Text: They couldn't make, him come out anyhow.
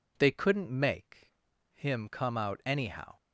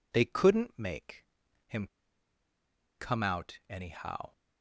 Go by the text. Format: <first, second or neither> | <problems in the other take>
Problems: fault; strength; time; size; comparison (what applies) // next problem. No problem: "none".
first | pauses between "him" and "come"; at 1.8 s; 1.1 s long